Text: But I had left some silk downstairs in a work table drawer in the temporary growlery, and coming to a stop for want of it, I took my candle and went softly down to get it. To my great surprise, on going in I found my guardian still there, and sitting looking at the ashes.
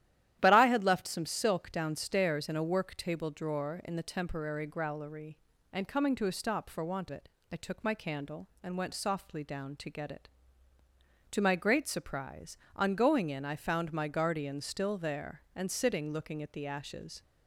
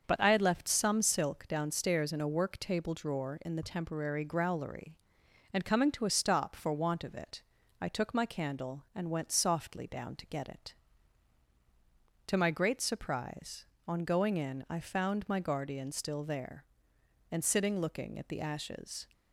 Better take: second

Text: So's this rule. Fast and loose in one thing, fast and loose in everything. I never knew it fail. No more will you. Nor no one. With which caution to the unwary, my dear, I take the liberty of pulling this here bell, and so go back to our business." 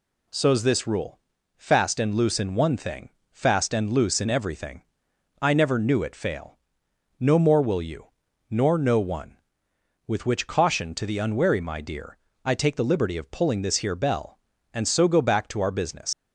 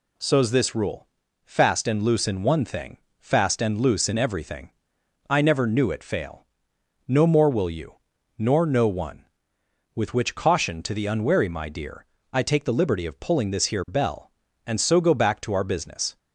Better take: second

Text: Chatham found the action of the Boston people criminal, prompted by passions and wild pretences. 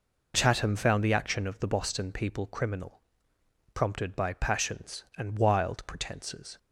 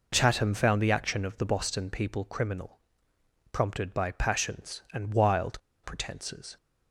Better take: first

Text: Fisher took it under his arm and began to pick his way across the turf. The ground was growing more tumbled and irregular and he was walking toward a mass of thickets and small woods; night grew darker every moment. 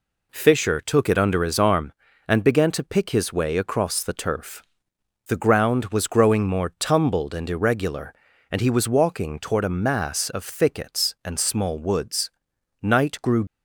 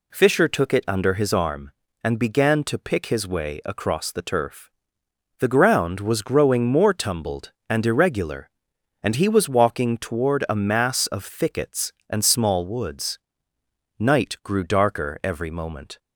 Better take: second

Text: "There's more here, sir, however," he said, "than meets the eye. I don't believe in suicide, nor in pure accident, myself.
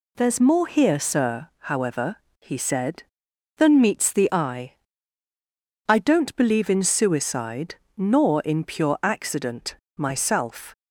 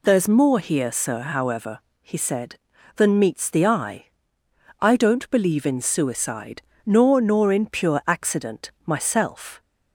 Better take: first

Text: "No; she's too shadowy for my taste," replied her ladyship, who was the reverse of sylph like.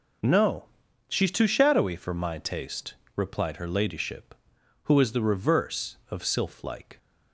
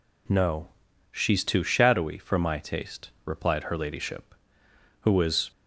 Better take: first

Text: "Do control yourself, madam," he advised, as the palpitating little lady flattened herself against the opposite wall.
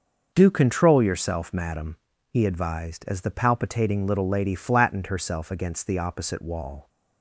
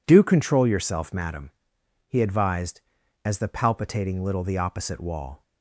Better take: first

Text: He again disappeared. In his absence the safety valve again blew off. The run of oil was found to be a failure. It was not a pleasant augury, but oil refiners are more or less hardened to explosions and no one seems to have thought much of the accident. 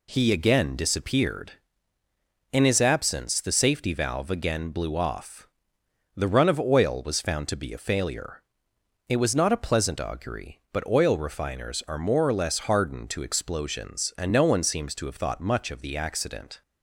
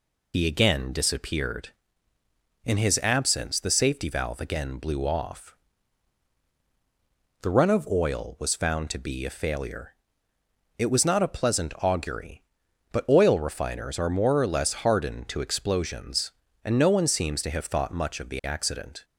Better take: first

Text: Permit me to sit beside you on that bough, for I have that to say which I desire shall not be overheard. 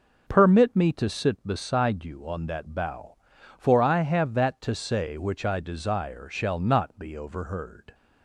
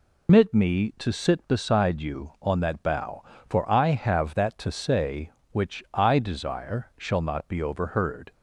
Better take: first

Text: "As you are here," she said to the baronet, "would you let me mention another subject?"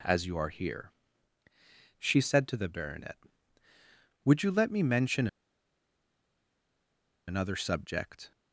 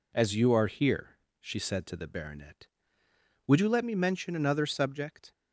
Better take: second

